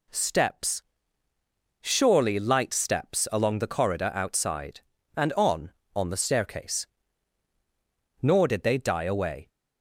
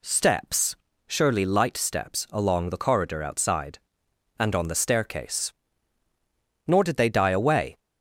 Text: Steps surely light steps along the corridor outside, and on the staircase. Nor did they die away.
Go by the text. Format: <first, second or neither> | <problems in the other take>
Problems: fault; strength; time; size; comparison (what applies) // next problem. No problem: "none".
second | pauses between "Steps" and "surely"; at 0.8 s; 1.0 s long; slight in the second // says "on" twice; at 5.9 s